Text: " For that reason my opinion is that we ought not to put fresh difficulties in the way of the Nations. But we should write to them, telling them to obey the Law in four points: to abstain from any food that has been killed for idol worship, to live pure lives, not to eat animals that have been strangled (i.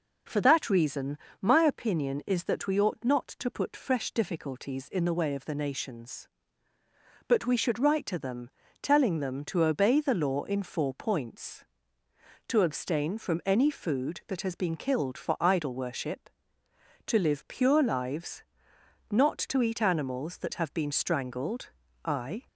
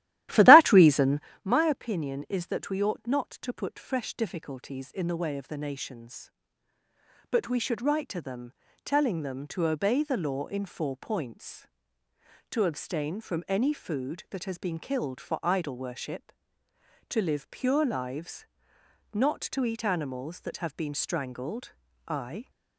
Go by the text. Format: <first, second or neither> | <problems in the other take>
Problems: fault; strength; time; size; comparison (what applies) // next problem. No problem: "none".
first | starts louder than the rest; strong; until 1.3 s; 14.5 dB // pauses between "reason" and "my"; slight; at 1.1 s; 0.24 s long; slight in the first